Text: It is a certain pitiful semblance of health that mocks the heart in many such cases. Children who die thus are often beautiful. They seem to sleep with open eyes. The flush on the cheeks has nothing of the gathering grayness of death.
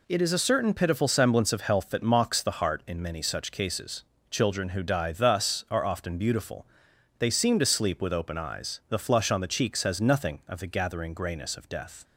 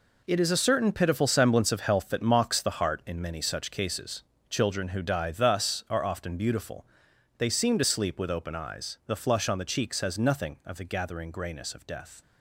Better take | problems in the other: first | gets quieter; strong; throughout; 11 dB

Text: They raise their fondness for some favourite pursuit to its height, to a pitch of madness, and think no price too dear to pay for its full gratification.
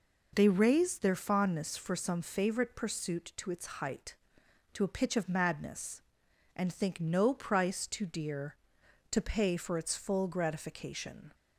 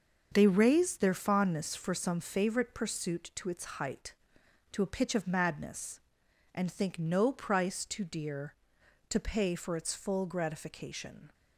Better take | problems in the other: first | gets quieter; strong; throughout; 8 dB

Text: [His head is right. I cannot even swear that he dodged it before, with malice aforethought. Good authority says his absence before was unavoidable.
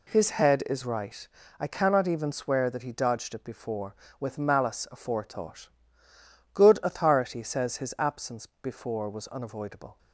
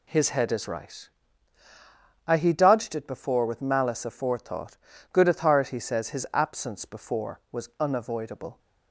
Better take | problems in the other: first | skips "cannot even swear that"; at 2.3 s

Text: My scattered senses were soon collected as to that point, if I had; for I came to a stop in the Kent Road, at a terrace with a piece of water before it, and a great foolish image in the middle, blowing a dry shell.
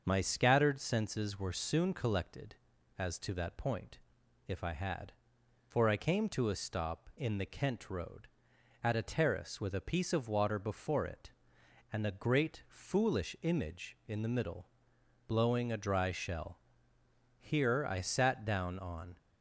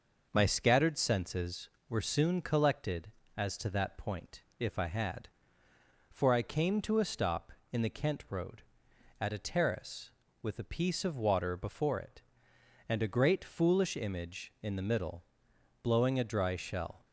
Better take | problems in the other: second | starts louder than the rest; until 1.0 s; 6.5 dB // goes on to say "Here I sat down on"; strong; from 17.3 s on; 1.7 s long

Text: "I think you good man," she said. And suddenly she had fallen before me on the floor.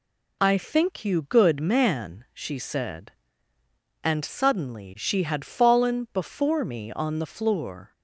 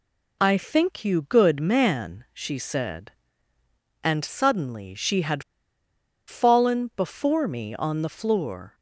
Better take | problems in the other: first | pauses between "had" and "fallen"; noticeable; at 5.4 s; 0.85 s long

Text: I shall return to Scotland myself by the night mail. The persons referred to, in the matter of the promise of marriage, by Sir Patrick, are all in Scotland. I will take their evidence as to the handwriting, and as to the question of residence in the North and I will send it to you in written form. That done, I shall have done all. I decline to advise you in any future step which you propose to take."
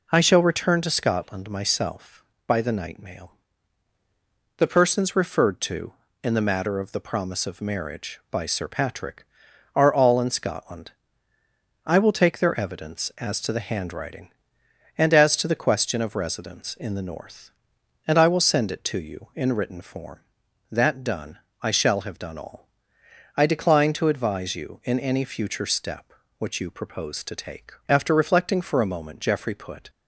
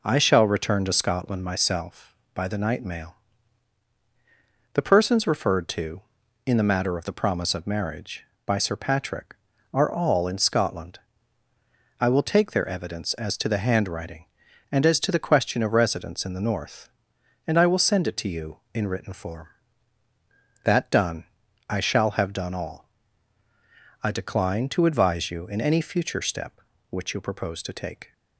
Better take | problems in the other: second | goes on to say "After reflecting for a moment Geoffrey put"; strong; from 27.8 s on; 2.0 s long

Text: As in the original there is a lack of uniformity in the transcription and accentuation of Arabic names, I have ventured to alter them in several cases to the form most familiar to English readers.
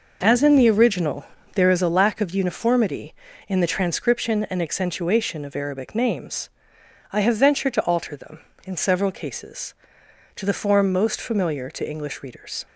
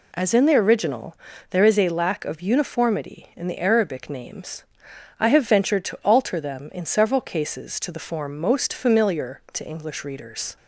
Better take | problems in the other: first | pauses between "original" and "there"; slight; at 1.1 s; 0.34 s long; slight in the first // skips "transcription and accentuation of"; at 3.5 s

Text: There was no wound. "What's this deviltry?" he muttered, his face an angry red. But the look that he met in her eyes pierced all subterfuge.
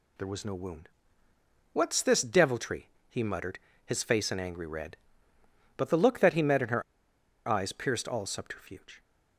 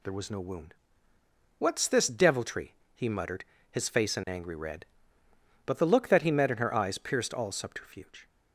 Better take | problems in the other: second | pauses between "her" and "eyes"; noticeable; at 6.8 s; 0.64 s long

